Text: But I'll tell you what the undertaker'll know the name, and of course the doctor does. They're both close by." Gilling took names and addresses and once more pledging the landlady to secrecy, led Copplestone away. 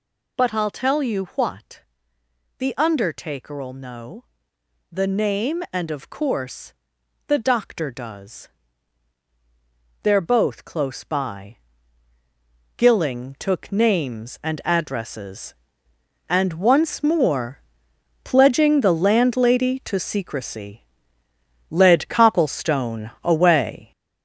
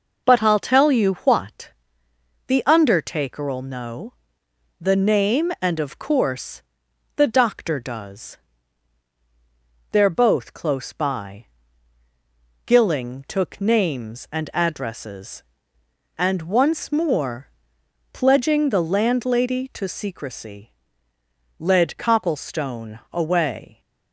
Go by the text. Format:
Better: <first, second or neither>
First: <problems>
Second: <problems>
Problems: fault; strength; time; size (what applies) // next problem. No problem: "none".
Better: second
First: gets louder; noticeable; throughout; 6 dB // pauses between "what" and "the"; noticeable; at 1.8 s; 0.76 s long // pauses between "know" and "the"; noticeable; at 4.2 s; 0.66 s long // pauses between "course" and "the"; noticeable; at 6.7 s; 0.54 s long // pauses between "more" and "pledging"; noticeable; at 17.5 s; 0.64 s long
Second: pauses between "what" and "the"; noticeable; at 1.6 s; 0.76 s long // pauses between "know" and "the"; noticeable; at 4.1 s; 0.66 s long // pauses between "course" and "the"; noticeable; at 6.6 s; 0.54 s long // pauses between "more" and "pledging"; noticeable; at 17.4 s; 0.64 s long